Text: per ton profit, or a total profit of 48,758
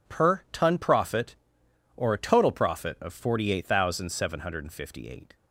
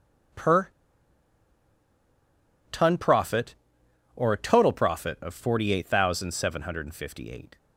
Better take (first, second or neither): first